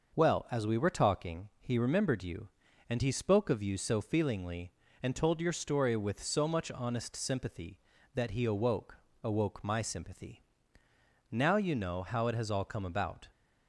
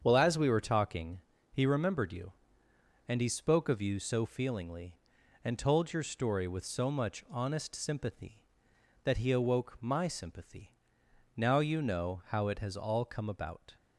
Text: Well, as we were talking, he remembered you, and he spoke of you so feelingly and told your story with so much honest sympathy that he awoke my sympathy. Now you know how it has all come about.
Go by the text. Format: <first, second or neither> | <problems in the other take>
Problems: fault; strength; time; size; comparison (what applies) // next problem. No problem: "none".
second | starts louder than the rest; until 1.1 s; 6 dB; strong in the second // says "awoke" twice; at 9.2 s